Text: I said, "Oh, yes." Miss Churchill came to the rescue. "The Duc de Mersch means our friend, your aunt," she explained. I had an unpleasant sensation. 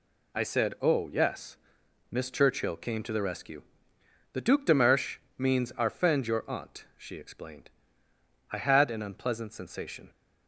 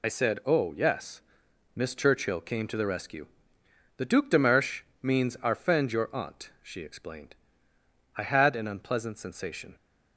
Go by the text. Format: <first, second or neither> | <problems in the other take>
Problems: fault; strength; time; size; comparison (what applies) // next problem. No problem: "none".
first | loses the start of "I"; at 0.0 s; 35 ms // pauses between "Mersch" and "means"; slight; at 4.8 s; 0.22 s long; slight in the first